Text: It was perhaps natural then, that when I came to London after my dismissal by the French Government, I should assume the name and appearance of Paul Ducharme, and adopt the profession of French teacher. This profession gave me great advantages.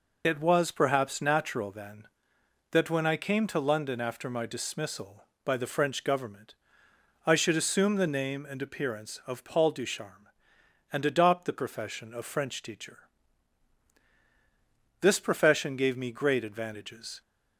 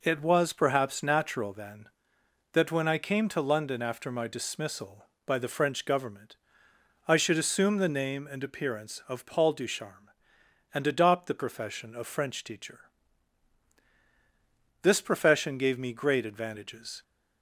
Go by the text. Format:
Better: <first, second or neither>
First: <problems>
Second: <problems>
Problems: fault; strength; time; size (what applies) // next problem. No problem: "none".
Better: second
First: loses the start of "It"; at 0.2 s; 40 ms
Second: none